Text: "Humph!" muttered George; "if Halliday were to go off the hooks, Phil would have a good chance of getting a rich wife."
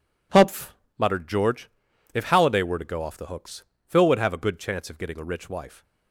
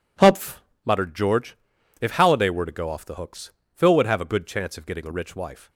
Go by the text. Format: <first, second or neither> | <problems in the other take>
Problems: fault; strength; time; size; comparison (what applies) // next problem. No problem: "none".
neither | none